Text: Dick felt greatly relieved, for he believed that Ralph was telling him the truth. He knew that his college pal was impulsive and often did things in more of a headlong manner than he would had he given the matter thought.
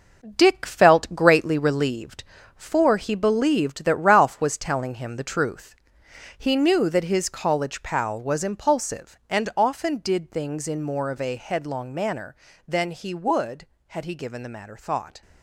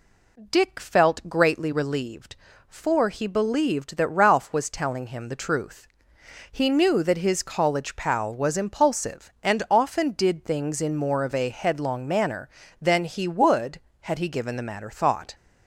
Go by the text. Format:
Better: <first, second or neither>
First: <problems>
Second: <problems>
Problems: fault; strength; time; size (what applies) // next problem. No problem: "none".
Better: second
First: gets quieter; strong; throughout; 8 dB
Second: none